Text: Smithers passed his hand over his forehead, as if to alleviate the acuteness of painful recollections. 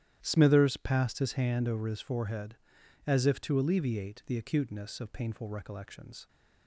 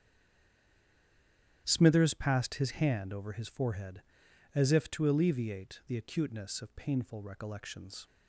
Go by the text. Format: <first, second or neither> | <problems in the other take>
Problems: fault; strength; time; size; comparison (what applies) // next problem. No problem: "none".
first | stays silent before the first word; noticeable; until 1.6 s; 1.6 s long // starts louder than the rest; strong; until 2.6 s; 11 dB; strong in the first